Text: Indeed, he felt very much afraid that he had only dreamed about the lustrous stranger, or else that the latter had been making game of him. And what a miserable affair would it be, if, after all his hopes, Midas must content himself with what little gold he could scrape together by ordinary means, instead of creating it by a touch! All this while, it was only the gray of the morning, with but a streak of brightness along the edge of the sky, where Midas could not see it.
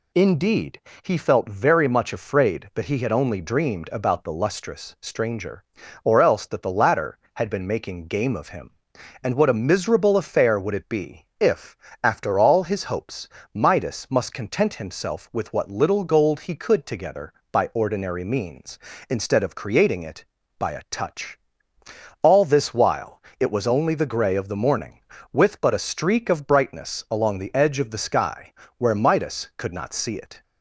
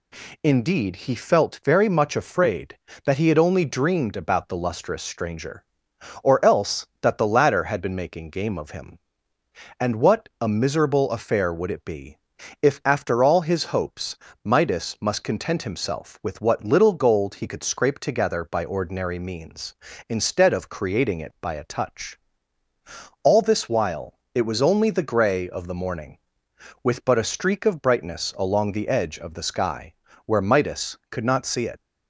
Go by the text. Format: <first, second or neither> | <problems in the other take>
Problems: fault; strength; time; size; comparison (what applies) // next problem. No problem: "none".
second | skips "scrape"; at 16.8 s